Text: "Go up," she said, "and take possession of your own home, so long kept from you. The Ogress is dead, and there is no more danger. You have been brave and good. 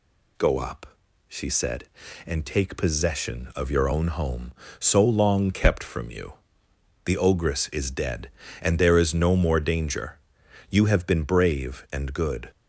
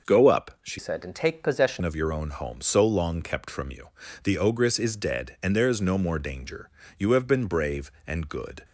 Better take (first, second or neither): first